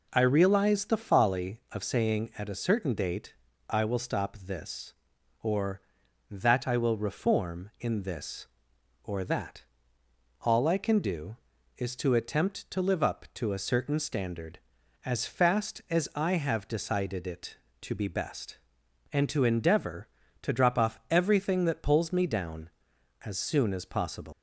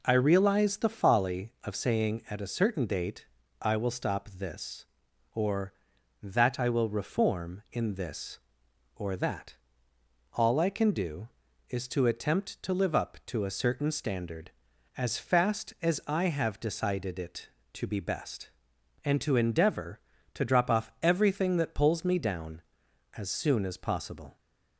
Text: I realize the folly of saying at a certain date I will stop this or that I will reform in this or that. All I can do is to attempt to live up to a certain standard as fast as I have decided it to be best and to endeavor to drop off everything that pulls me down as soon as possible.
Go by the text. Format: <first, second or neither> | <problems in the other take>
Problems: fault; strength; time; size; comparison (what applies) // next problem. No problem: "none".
second | pauses between "date" and "I"; slight; at 3.3 s; 0.34 s long; slight in the second // leaves "possible" unfinished; at 24.3 s; 135 ms